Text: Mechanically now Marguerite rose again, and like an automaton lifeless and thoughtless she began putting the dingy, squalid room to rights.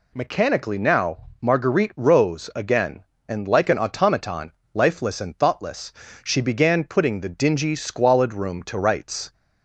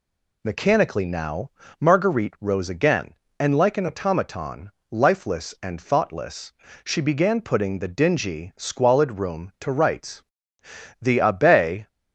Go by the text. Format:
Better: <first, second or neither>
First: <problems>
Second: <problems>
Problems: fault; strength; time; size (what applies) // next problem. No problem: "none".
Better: first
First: pauses between "now" and "Marguerite"; slight; at 1.1 s; 0.20 s long // pauses between "automaton" and "lifeless"; slight; at 4.5 s; 0.20 s long // pauses between "thoughtless" and "she"; slight; at 5.9 s; 0.32 s long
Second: pauses between "now" and "Marguerite"; slight; at 1.5 s; 0.30 s long // pauses between "automaton" and "lifeless"; slight; at 4.7 s; 0.18 s long // pauses between "thoughtless" and "she"; slight; at 6.5 s; 0.32 s long // goes on to say "The Abbe"; noticeable; from 11.0 s on; 0.86 s long